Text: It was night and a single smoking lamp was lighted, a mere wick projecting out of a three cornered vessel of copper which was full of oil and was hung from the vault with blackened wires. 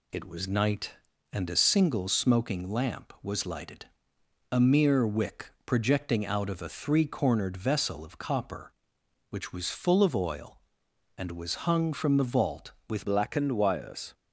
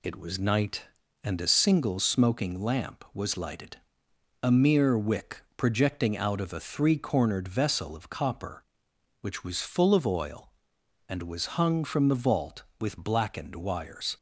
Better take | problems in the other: second | pauses between "wick" and "projecting"; slight; at 5.5 s; 0.16 s long; slight in the second // changes voice at "blackened"; from 13.0 s on; 1.1 s long

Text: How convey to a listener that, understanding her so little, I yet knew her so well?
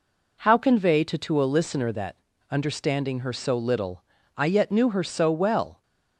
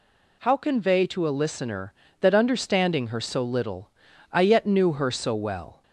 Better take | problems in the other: second | says "to" twice; at 1.1 s

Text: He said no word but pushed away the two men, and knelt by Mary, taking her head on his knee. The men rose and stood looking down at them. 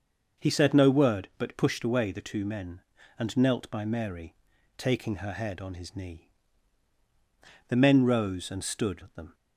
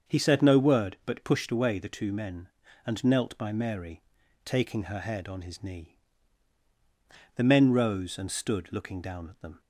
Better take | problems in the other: second | starts louder than the rest; until 1.4 s; 6 dB; also in the second // skips "looking down"; at 9.0 s

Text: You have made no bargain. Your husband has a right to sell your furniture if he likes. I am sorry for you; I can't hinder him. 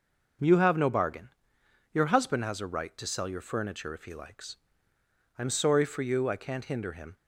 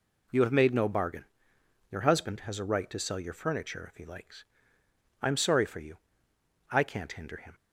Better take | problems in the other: second | skips "made"; at 0.7 s

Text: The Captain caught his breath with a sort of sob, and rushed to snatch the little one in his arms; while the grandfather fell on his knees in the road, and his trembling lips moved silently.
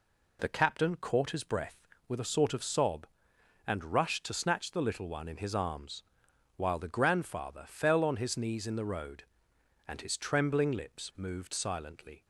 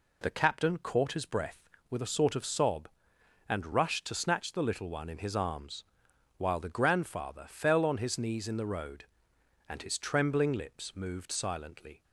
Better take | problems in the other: neither | none

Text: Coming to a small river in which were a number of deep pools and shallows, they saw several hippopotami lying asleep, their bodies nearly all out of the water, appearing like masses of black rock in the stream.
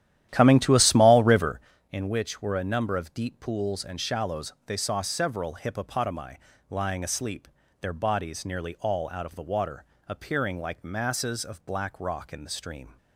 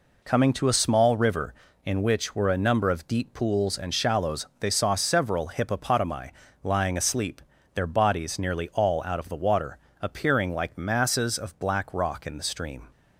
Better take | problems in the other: second | starts louder than the rest; strong; until 1.7 s; 12 dB // pauses between "hippopotami" and "lying"; slight; at 6.3 s; 0.32 s long; slight in the second

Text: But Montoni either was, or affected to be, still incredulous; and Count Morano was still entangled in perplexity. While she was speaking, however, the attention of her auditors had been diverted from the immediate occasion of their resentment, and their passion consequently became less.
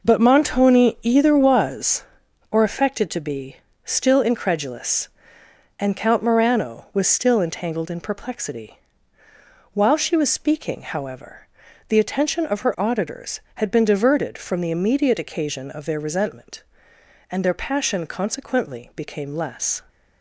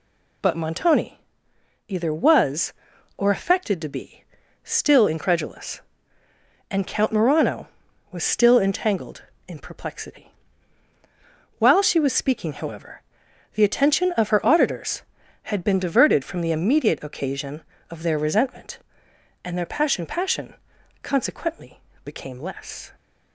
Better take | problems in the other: first | pauses between "Montoni" and "either"; noticeable; at 1.1 s; 0.68 s long // says "passion" twice; at 20.0 s // pauses between "consequently" and "became"; slight; at 21.8 s; 0.24 s long

